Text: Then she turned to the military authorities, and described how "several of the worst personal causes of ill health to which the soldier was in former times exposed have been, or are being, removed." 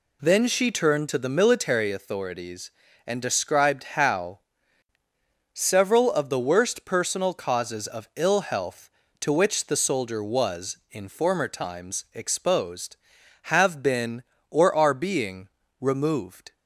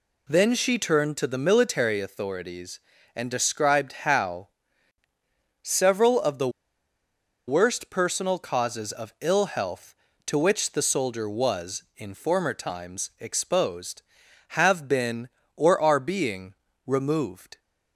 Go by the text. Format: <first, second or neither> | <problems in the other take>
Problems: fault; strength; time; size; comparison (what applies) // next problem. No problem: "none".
first | pauses between "described" and "how"; slight; at 3.9 s; 0.16 s long; slight in the first // pauses between "how" and "several"; at 4.4 s; 1.1 s long; also in the first // pauses between "the" and "worst"; at 6.4 s; 0.98 s long